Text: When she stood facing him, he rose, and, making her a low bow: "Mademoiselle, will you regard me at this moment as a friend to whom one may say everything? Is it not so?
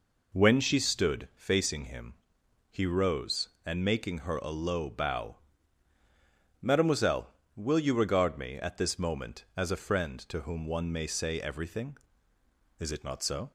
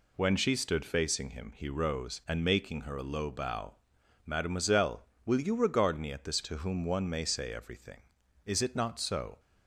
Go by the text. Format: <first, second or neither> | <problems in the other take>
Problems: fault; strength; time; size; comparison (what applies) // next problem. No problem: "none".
first | skips "moment as a friend"; at 6.4 s